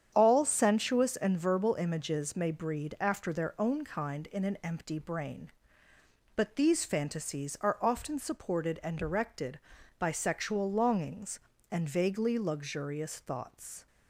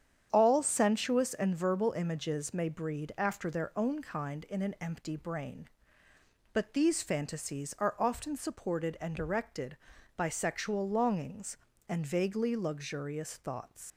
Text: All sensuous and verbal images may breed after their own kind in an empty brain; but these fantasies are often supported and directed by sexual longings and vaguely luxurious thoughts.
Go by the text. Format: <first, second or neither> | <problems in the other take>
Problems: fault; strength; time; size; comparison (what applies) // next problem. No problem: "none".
first | starts louder than the rest; strong; until 1.3 s; 8.5 dB; strong in the first // leaves "thoughts" unfinished; at 13.9 s; 135 ms